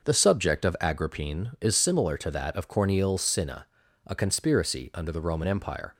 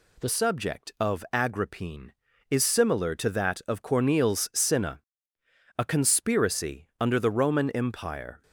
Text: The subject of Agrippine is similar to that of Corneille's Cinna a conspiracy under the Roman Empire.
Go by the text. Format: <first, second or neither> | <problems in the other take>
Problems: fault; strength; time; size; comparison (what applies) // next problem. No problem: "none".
first | changes voice at "subject"; from 0.2 s on; 8.2 s long // pauses between "Cinna" and "a"; noticeable; at 5.0 s; 0.78 s long; also in the first